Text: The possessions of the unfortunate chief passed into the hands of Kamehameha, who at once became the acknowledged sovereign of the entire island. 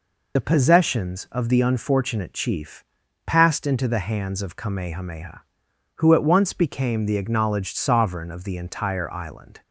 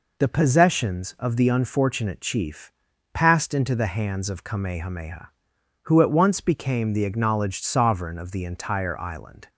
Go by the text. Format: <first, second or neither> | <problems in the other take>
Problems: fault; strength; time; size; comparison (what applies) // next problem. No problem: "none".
second | loses the start of "The"; at 0.3 s; 35 ms // pauses between "chief" and "passed"; at 2.8 s; 0.42 s long; also in the second